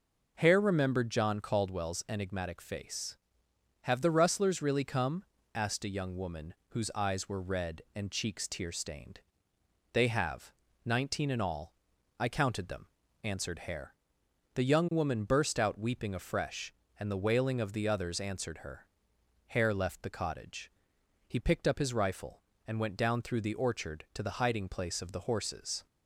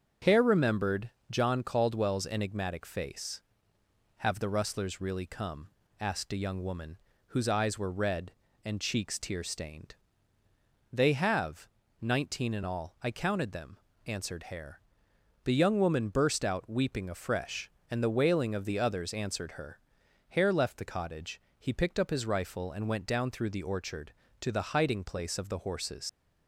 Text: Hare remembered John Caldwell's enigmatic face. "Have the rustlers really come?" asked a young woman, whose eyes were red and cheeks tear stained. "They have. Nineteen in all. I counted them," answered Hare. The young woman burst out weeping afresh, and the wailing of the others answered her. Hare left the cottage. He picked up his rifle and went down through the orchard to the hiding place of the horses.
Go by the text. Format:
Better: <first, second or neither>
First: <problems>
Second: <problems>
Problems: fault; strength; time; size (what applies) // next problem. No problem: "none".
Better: first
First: none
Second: starts louder than the rest; until 1.4 s; 6.5 dB // pauses between "remembered" and "John"; slight; at 1.1 s; 0.20 s long // leaves "horses" unfinished; at 26.0 s; 90 ms